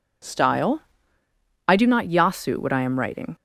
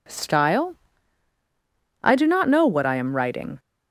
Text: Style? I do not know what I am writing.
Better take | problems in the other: second | says "yasu" for "know"; at 2.0 s

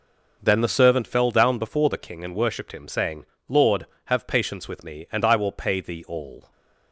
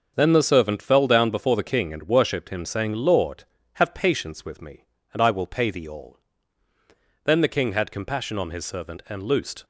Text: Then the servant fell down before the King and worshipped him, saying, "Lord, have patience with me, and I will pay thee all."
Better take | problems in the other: first | starts louder than the rest; until 1.1 s; 6 dB // goes on to say "Then the King had compassion on his servant and loosed"; strong; from 7.2 s on; 2.4 s long

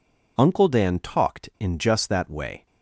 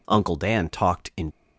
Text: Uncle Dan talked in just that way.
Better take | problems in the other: first | stops before "just that way"; at 1.3 s

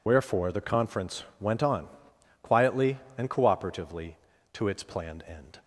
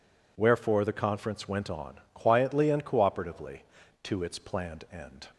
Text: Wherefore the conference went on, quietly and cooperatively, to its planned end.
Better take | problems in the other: second | loses the start of "Wherefore"; at 0.0 s; 40 ms // pauses between "conference" and "went"; slight; at 1.2 s; 0.16 s long

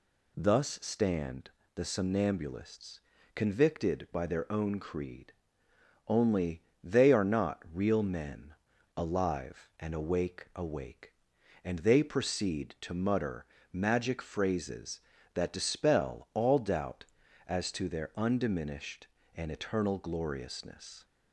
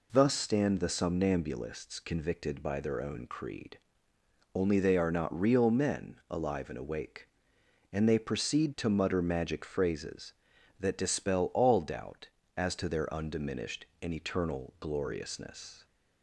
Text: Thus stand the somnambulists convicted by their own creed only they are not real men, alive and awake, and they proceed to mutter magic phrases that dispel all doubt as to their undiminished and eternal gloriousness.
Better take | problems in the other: second | pauses between "stand" and "the"; slight; at 1.5 s; 0.26 s long // pauses between "somnambulists" and "convicted"; slight; at 2.9 s; 0.36 s long // pauses between "creed" and "only"; noticeable; at 5.3 s; 0.76 s long; noticeable in the second // pauses between "only" and "they"; slight; at 6.6 s; 0.22 s long // says "awake" twice; at 10.5 s // pauses between "mutter" and "magic"; slight; at 13.4 s; 0.26 s long

